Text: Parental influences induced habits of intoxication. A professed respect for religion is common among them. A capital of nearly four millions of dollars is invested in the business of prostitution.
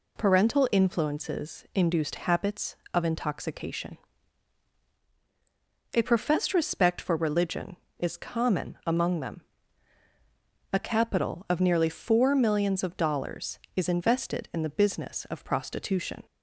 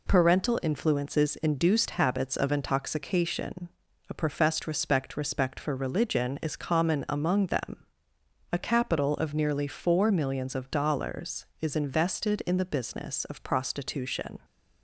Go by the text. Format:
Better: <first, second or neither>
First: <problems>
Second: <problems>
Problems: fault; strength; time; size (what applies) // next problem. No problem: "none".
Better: first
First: none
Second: says "respect" twice; at 5.1 s